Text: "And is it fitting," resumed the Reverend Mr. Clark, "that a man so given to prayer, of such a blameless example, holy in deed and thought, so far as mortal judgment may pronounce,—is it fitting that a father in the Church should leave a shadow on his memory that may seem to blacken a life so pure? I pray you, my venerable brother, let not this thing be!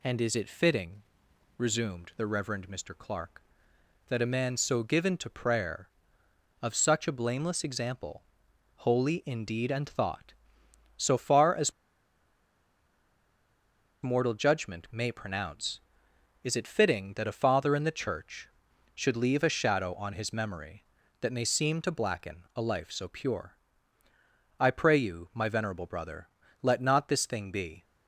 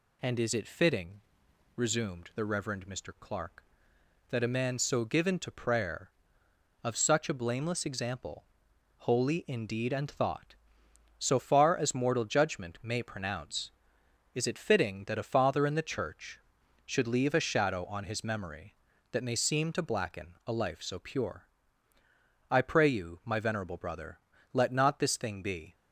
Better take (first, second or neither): second